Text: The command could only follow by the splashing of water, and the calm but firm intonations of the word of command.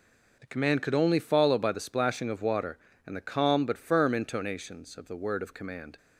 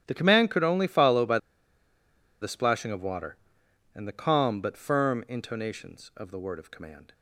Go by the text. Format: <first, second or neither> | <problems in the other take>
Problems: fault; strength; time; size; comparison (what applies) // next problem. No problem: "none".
first | starts louder than the rest; strong; until 1.0 s; 10.5 dB // pauses between "by" and "the"; at 1.3 s; 1.0 s long